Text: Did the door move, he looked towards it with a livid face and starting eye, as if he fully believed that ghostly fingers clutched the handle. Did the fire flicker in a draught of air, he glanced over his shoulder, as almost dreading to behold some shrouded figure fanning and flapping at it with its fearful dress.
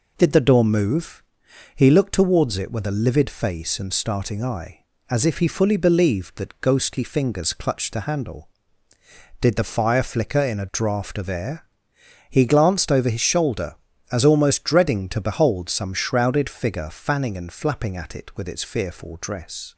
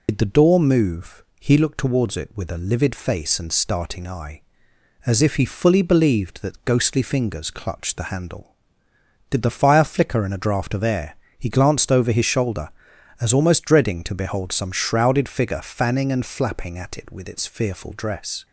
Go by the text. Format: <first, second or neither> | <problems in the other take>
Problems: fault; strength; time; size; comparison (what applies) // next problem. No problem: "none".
first | loses the start of "Did"; at 0.0 s; 85 ms